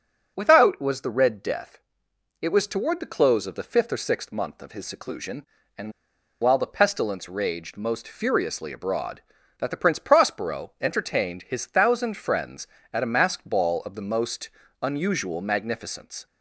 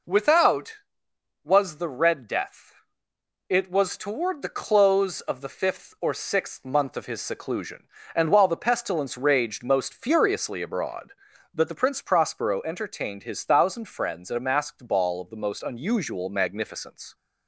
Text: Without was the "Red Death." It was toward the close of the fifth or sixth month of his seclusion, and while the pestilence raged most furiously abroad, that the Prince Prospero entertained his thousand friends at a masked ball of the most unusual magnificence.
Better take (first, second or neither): second